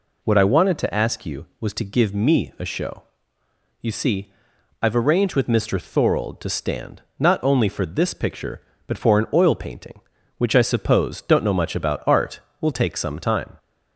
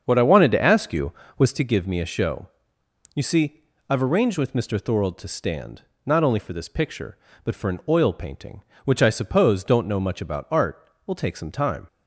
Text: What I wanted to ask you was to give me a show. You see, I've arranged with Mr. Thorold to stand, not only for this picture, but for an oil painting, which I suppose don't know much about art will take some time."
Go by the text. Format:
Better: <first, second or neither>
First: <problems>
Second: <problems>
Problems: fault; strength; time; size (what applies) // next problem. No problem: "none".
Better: first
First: none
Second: starts louder than the rest; strong; until 1.7 s; 7 dB